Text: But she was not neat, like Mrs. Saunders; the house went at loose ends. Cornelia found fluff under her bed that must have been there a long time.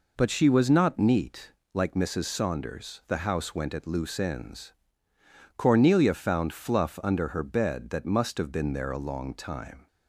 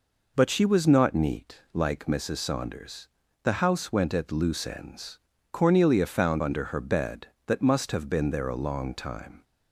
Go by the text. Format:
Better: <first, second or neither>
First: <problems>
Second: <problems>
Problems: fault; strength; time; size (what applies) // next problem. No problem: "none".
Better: first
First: none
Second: skips "fluff"; at 6.4 s